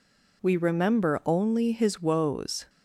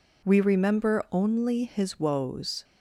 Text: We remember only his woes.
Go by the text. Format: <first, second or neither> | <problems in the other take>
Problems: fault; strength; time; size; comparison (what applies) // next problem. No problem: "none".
neither | none